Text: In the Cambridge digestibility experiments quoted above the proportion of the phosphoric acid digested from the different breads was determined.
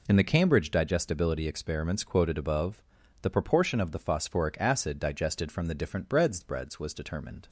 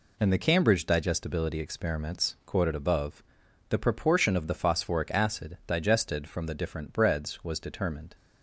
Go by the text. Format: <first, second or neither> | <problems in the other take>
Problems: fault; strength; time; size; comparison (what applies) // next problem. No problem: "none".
second | pauses between "above" and "the"; at 2.8 s; 0.42 s long; noticeable in the second // says "breads" twice; at 6.4 s